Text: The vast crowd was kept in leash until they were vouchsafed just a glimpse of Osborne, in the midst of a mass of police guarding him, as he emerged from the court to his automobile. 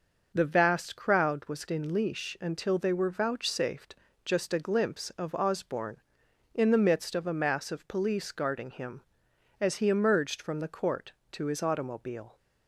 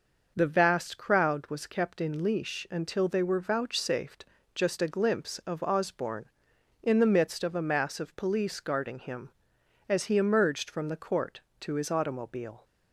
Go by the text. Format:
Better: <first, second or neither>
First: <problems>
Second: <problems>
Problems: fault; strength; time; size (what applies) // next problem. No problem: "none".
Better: second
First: skips "kept"; at 1.6 s // pauses between "vouchsafed" and "just"; slight; at 3.9 s; 0.32 s long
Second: pauses between "vouchsafed" and "just"; slight; at 4.2 s; 0.32 s long